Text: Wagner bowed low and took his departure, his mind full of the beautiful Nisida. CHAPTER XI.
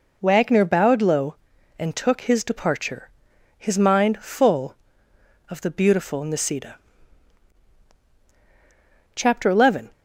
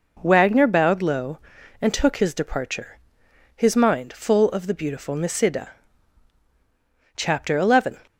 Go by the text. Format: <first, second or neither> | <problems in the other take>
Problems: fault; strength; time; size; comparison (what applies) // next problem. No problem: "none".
neither | none